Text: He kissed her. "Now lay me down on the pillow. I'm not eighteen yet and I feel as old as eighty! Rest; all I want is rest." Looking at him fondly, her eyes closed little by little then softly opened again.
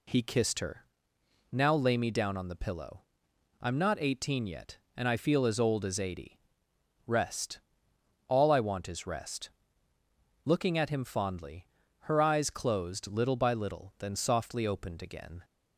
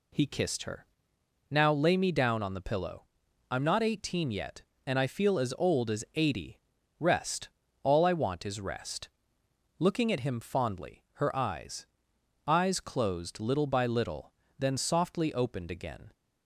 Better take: first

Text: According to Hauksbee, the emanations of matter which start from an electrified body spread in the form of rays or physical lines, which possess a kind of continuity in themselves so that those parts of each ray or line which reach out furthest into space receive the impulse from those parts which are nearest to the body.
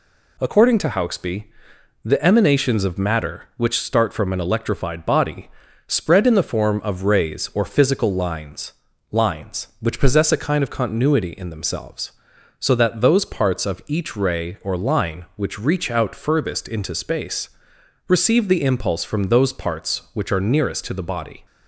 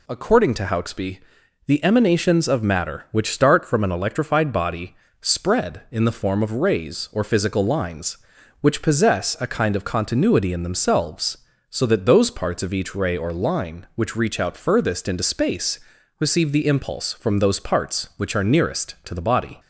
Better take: second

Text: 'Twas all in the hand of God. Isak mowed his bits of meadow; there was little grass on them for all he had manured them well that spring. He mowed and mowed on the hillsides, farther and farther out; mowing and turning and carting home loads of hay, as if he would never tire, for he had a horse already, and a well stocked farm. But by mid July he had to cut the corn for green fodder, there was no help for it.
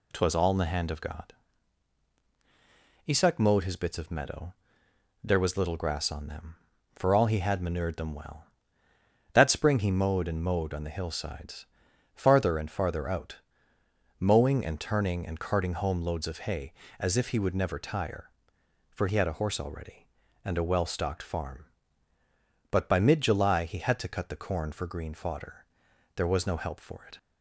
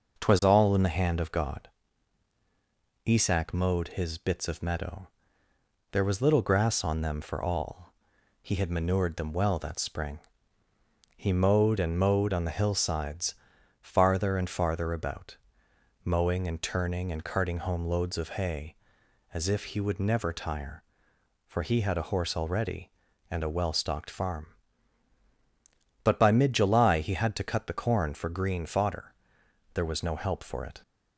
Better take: first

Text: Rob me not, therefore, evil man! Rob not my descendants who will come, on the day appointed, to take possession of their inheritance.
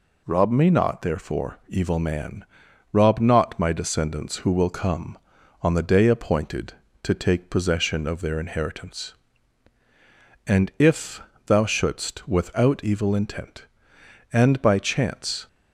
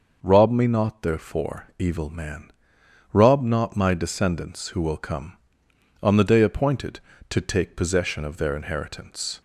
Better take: second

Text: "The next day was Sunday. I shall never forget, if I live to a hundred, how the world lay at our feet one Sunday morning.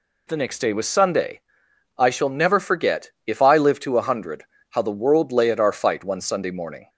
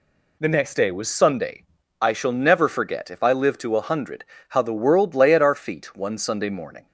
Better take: second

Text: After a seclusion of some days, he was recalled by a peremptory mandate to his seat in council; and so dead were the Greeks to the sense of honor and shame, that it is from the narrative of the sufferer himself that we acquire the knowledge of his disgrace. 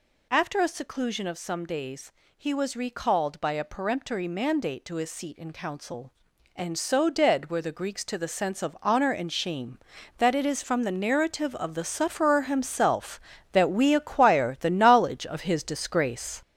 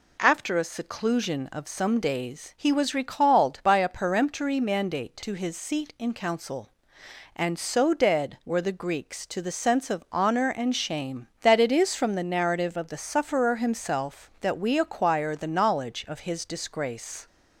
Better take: second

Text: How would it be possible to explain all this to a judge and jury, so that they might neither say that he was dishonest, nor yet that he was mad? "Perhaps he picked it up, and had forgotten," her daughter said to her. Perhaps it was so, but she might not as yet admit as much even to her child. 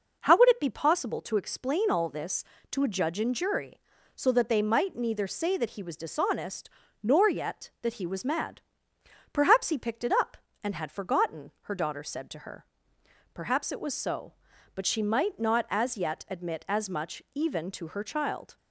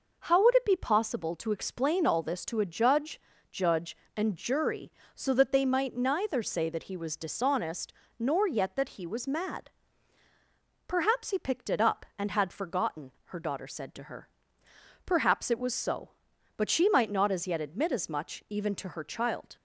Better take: first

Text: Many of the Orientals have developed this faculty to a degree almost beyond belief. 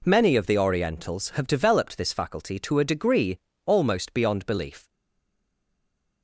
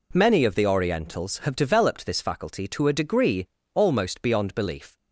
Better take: second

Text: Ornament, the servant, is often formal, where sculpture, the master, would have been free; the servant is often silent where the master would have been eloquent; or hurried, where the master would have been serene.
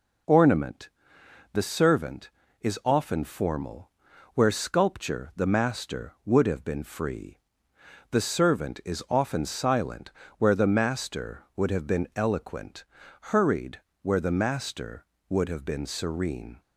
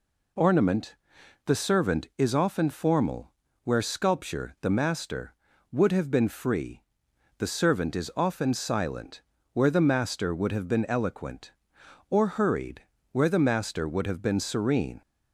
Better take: second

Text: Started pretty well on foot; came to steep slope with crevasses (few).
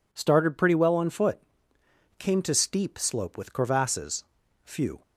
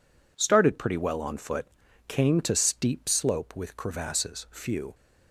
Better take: neither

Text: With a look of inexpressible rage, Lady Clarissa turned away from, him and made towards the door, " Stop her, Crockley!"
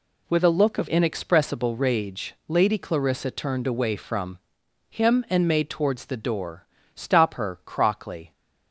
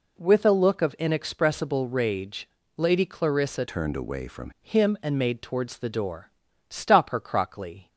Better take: first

